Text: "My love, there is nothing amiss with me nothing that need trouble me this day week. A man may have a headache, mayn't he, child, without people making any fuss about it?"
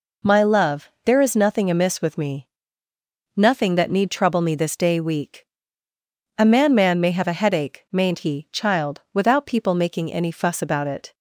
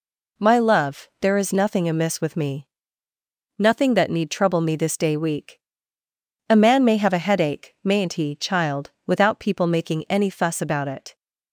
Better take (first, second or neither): second